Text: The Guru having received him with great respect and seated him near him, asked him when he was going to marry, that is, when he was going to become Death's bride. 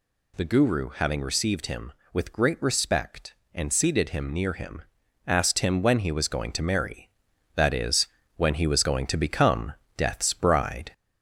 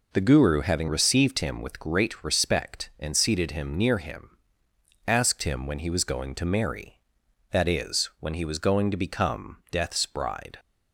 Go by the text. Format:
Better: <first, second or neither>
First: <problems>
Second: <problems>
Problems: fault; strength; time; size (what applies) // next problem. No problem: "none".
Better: second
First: gets louder; slight; throughout; 3 dB // pauses between "become" and "Death's"; slight; at 9.7 s; 0.24 s long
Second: none